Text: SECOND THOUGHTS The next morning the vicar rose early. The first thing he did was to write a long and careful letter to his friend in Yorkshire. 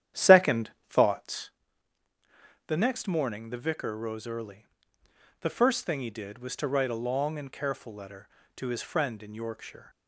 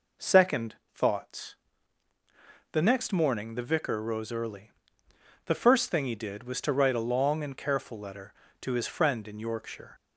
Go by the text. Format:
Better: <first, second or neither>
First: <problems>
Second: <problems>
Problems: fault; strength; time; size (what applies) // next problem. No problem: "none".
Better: second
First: starts louder than the rest; strong; until 1.6 s; 10.5 dB // pauses between "SECOND" and "THOUGHTS"; slight; at 0.6 s; 0.22 s long // pauses between "THOUGHTS" and "The"; at 1.4 s; 1.1 s long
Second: pauses between "SECOND" and "THOUGHTS"; slight; at 0.7 s; 0.22 s long // pauses between "THOUGHTS" and "The"; at 1.5 s; 1.1 s long